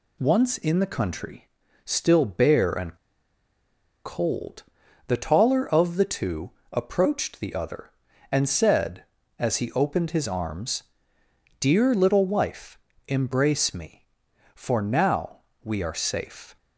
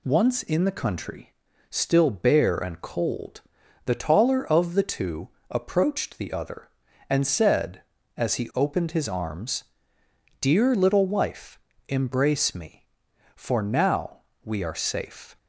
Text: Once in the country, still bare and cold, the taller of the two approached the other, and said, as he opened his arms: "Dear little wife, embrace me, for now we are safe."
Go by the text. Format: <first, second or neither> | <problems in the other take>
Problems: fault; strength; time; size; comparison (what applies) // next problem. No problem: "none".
second | pauses between "and" and "cold"; at 2.9 s; 1.0 s long // pauses between "two" and "approached"; slight; at 6.5 s; 0.20 s long; slight in the second // pauses between "now" and "we"; slight; at 15.4 s; 0.24 s long; slight in the second